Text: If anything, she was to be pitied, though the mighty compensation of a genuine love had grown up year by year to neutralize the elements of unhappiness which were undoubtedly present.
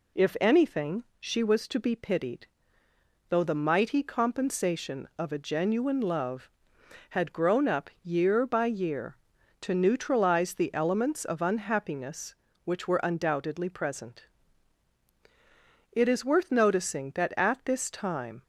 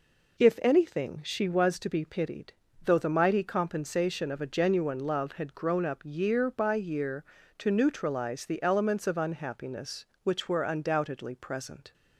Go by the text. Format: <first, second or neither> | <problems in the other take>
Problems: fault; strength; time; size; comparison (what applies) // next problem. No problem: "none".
second | goes on to say "It is worth noticing that at this time"; strong; from 15.9 s on; 2.5 s long